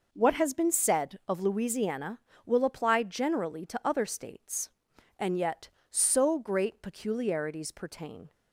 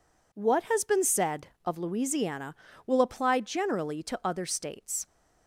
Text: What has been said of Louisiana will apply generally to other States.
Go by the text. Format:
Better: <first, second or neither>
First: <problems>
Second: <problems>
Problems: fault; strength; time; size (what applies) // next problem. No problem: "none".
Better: second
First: goes on to say "And yet so great peculiarities pertain"; strong; from 5.1 s on; 3.1 s long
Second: none